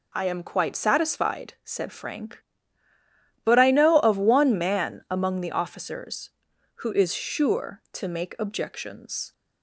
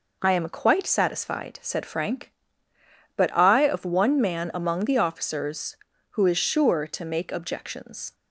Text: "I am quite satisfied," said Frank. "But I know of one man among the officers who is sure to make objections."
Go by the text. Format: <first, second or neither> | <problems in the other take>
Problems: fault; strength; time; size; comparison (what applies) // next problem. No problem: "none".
first | skips "know"; at 3.6 s